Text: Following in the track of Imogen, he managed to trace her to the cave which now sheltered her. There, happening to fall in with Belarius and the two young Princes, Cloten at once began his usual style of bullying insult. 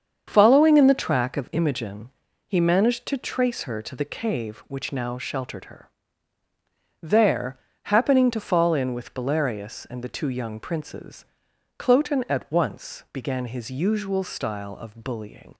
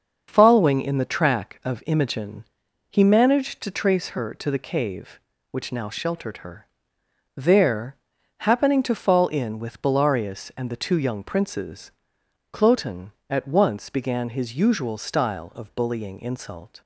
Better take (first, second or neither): second